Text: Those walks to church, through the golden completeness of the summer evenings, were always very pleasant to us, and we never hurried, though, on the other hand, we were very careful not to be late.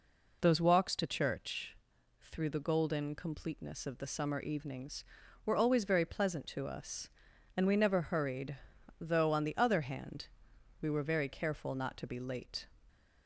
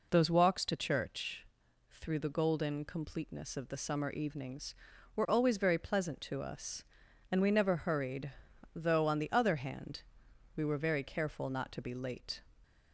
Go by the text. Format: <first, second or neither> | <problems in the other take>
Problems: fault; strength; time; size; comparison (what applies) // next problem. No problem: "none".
neither | none